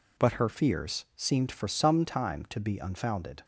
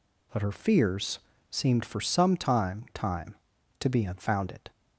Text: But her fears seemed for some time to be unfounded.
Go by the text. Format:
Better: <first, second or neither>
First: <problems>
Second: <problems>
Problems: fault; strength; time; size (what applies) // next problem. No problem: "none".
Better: first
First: none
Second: pauses between "fears" and "seemed"; slight; at 1.1 s; 0.32 s long // says "time" twice; at 2.9 s